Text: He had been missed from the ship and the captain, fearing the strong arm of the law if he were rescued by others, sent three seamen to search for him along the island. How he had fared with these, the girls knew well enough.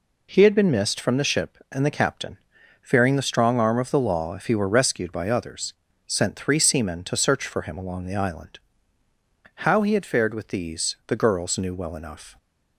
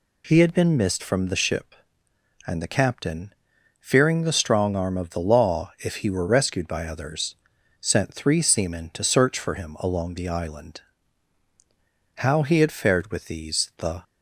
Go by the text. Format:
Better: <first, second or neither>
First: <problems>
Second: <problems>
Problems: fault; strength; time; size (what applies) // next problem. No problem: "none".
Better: first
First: none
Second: stops before "girls knew well enough"; at 14.0 s